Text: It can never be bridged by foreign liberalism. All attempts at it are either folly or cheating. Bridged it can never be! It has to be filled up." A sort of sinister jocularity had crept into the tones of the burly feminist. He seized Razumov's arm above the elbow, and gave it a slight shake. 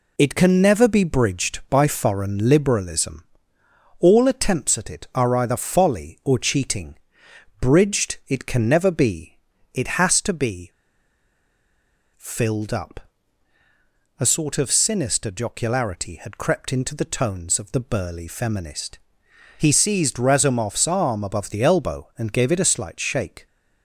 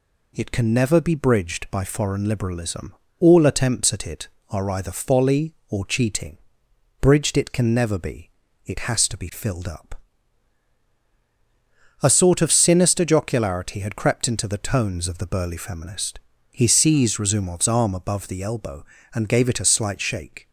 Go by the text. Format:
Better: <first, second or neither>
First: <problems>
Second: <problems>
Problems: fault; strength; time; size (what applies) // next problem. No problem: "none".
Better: second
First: pauses between "be" and "filled"; strong; at 10.7 s; 1.4 s long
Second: none